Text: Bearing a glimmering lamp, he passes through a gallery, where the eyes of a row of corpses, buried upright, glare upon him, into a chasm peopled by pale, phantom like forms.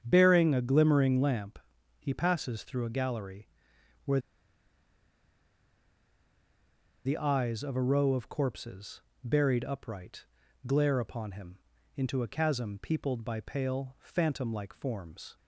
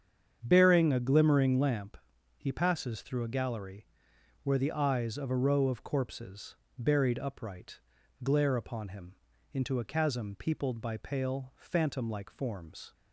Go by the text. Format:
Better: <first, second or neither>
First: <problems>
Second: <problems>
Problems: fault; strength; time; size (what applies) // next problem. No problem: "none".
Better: second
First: starts louder than the rest; strong; until 1.0 s; 8 dB // pauses between "where" and "the"; strong; at 4.1 s; 2.8 s long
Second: starts louder than the rest; strong; until 1.4 s; 8 dB